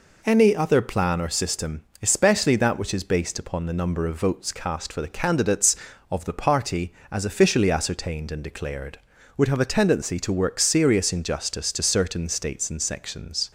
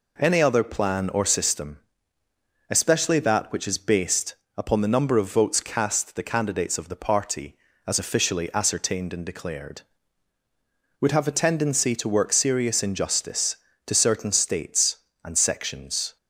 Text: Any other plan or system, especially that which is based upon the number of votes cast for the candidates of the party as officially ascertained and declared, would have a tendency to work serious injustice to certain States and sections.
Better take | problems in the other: first | pauses between "based" and "upon"; slight; at 4.3 s; 0.22 s long // skips "for"; at 6.1 s

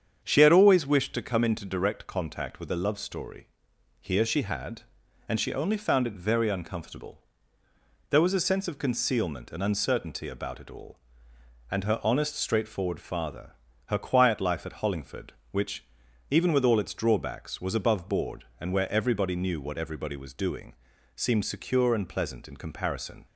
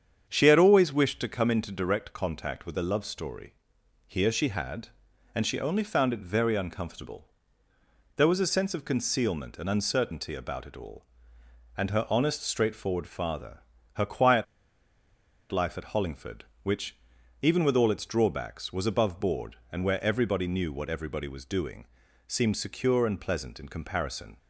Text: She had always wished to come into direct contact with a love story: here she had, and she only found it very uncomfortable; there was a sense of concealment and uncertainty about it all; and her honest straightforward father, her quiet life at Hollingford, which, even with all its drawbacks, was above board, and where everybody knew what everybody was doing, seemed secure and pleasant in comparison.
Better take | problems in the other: first | starts louder than the rest; strong; until 1.3 s; 8 dB; strong in the first // pauses between "quiet" and "life"; at 14.4 s; 1.0 s long

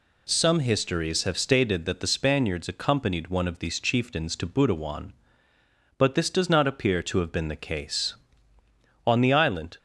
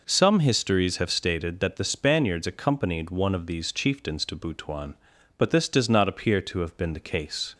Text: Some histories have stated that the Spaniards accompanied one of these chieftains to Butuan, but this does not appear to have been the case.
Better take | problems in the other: second | goes on to say "On the island"; noticeable; from 9.0 s on; 0.72 s long

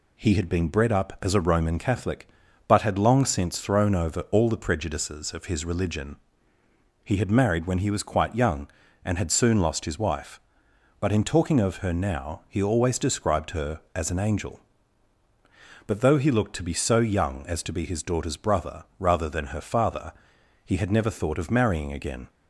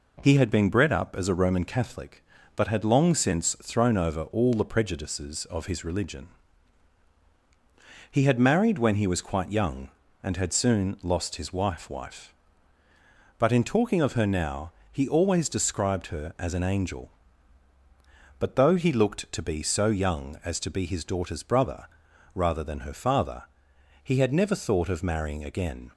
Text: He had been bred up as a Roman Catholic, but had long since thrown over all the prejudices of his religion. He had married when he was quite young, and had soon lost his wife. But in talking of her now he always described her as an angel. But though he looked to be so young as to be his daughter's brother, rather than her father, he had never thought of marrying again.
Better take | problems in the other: first | says "wife" twice; at 11.8 s // pauses between "now" and "he"; slight; at 14.7 s; 0.18 s long

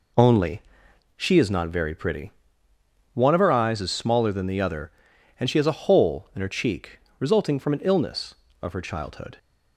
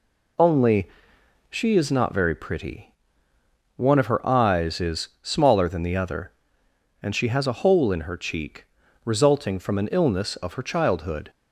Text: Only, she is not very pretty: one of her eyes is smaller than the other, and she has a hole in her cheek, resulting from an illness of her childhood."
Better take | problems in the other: neither | none

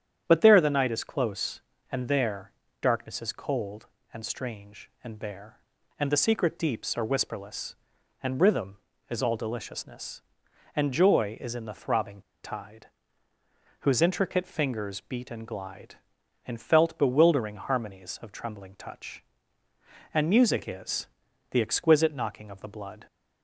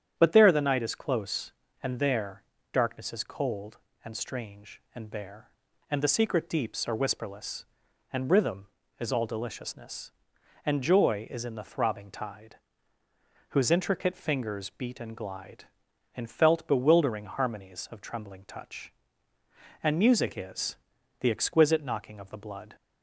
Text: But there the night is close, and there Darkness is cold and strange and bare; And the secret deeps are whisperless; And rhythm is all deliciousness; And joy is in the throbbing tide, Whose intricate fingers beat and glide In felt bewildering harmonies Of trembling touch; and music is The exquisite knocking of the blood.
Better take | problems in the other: second | starts louder than the rest; strong; until 1.2 s; 9 dB; strong in the second // pauses between "there" and "Darkness"; slight; at 2.5 s; 0.30 s long; slight in the second // pauses between "throbbing" and "tide"; slight; at 12.2 s; 0.21 s long // pauses between "is" and "The"; noticeable; at 21.0 s; 0.46 s long; noticeable in the second

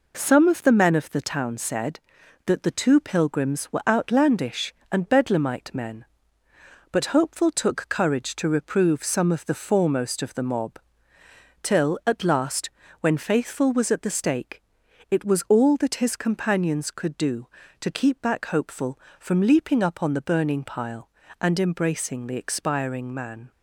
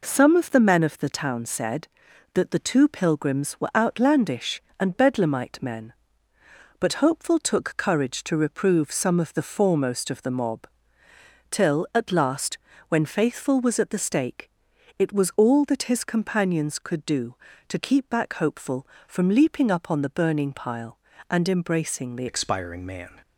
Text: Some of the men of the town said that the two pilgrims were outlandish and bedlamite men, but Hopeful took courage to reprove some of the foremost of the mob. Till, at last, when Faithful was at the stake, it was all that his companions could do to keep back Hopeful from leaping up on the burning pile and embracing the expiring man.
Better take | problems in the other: first | changes voice at "expiring"; from 22.2 s on; 1.0 s long

